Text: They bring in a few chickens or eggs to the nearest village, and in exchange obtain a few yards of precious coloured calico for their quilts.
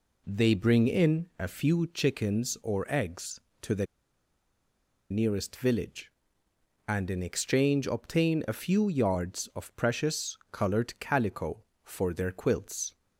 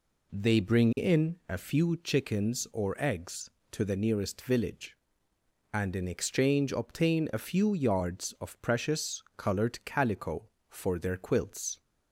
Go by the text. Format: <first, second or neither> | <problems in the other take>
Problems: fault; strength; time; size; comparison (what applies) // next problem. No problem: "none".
second | pauses between "the" and "nearest"; strong; at 3.8 s; 1.2 s long